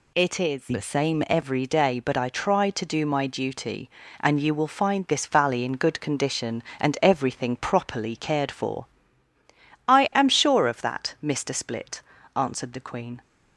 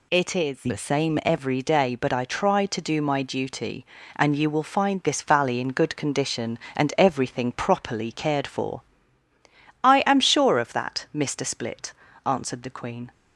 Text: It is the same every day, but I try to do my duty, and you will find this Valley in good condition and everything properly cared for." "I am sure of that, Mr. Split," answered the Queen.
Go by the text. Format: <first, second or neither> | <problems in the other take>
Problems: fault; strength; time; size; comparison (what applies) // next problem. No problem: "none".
neither | none